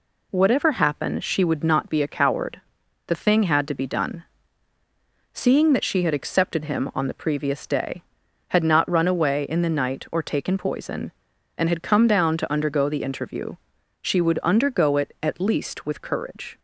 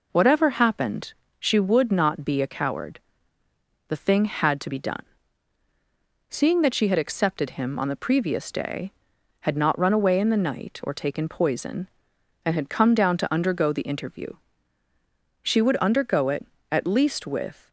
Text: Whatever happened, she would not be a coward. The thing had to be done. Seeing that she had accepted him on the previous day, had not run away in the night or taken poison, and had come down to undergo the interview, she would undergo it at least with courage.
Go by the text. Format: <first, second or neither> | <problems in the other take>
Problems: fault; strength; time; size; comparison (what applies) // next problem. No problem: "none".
first | stops before "courage"; at 17.6 s